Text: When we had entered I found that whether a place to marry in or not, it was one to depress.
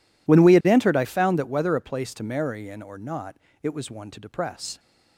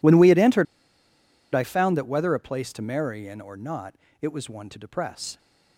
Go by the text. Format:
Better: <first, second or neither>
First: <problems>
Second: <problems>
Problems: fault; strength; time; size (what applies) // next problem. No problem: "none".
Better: first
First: none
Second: pauses between "entered" and "I"; noticeable; at 0.6 s; 0.88 s long